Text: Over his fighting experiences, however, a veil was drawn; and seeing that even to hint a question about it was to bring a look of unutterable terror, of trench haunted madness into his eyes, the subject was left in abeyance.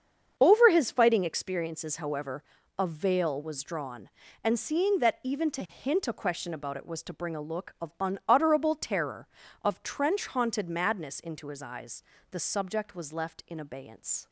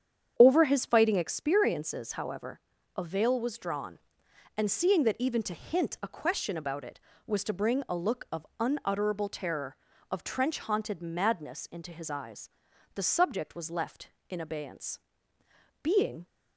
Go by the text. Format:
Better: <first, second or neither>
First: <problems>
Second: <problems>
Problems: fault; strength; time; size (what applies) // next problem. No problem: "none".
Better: first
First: starts louder than the rest; strong; until 1.3 s; 7 dB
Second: starts louder than the rest; strong; until 1.3 s; 8.5 dB // goes on to say "Being"; slight; from 15.8 s on; 0.44 s long